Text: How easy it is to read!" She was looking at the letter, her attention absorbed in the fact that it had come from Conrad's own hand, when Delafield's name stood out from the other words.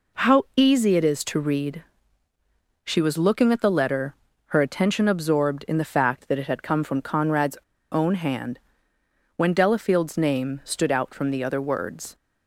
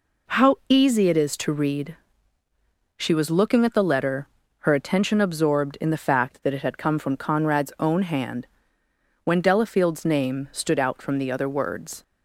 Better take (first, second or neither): second